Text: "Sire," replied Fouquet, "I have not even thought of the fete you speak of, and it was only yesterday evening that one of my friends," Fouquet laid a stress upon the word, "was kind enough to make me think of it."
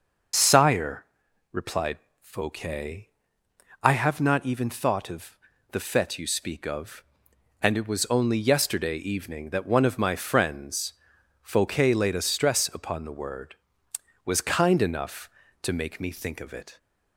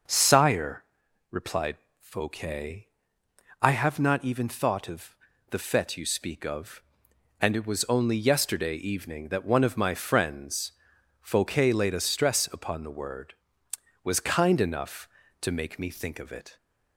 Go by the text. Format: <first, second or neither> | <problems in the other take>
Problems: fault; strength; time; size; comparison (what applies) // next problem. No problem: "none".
second | loses the start of "Sire"; at 0.3 s; 55 ms // pauses between "replied" and "Fouquet"; slight; at 1.9 s; 0.22 s long; slight in the second // pauses between "of" and "the"; slight; at 5.3 s; 0.34 s long; slight in the second